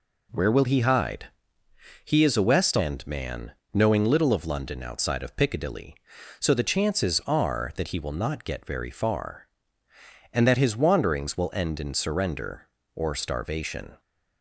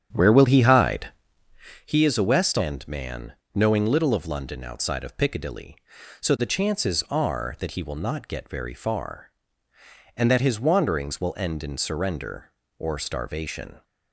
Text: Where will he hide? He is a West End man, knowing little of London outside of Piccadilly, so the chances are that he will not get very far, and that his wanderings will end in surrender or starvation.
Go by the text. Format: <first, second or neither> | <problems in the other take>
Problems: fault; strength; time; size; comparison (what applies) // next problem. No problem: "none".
first | starts louder than the rest; strong; until 1.9 s; 9 dB